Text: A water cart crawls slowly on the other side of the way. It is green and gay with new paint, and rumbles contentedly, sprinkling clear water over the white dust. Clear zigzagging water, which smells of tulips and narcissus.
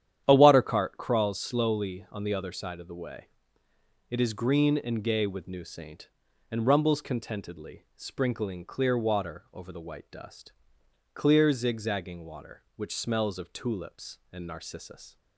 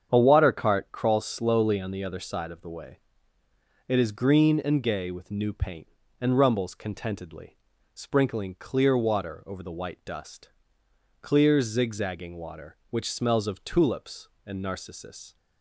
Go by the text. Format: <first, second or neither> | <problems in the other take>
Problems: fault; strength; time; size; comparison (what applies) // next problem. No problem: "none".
second | starts louder than the rest; strong; until 1.2 s; 10 dB; strong in the second // says "saint" for "paint"; at 5.6 s